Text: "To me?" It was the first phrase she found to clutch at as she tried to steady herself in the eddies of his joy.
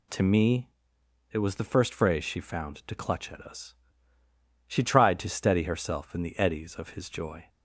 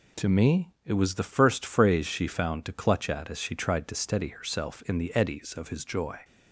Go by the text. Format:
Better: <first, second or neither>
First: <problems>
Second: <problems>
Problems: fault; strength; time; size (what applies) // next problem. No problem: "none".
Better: second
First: says "us" for "as"; at 3.4 s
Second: none